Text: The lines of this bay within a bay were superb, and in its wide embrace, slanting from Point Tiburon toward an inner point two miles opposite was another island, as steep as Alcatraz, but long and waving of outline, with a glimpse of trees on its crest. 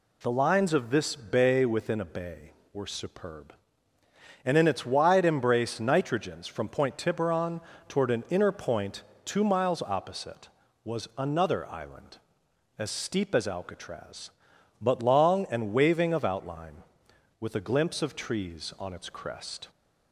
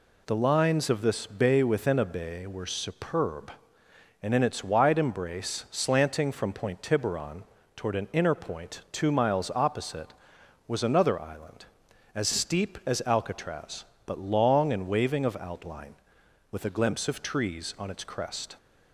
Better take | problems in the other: second | says "nitrogens" for "slanting"; at 5.7 s // pauses between "Tiburon" and "toward"; slight; at 7.5 s; 0.28 s long; slight in the second // pauses between "point" and "two"; slight; at 9.0 s; 0.22 s long

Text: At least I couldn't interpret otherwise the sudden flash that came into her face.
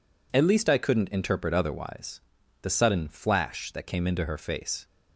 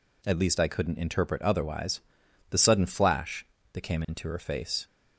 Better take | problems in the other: neither | pauses between "otherwise" and "the"; the same in both

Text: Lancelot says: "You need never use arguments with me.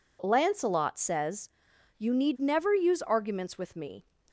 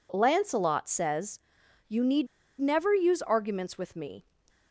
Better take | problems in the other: first | pauses between "need" and "never"; slight; at 2.2 s; 0.33 s long

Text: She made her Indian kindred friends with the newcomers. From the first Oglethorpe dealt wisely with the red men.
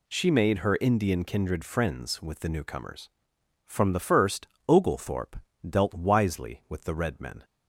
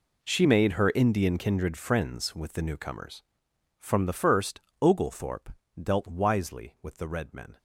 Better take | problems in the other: first | gets quieter; strong; throughout; 15.5 dB // pauses between "first" and "Oglethorpe"; slight; at 4.5 s; 0.22 s long; slight in the first // pauses between "Oglethorpe" and "dealt"; slight; at 5.4 s; 0.32 s long; slight in the first

